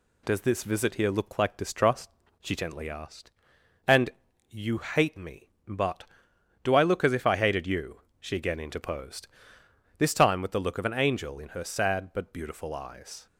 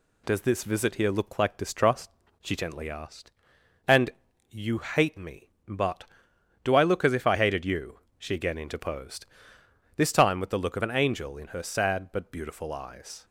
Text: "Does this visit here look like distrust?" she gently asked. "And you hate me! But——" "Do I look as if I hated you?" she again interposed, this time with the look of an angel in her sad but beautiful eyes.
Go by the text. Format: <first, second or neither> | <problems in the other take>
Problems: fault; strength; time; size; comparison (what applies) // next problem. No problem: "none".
neither | pauses between "And" and "you"; the same in both